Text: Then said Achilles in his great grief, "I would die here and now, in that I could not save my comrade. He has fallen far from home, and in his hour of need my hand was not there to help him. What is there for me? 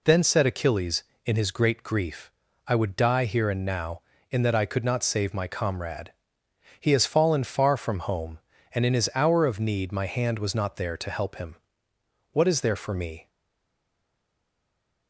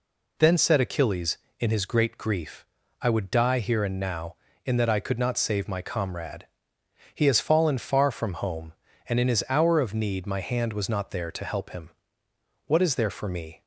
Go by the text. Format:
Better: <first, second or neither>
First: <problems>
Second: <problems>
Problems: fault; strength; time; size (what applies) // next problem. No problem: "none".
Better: second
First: stays silent after the last word; noticeable; from 13.2 s on; 1.8 s long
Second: none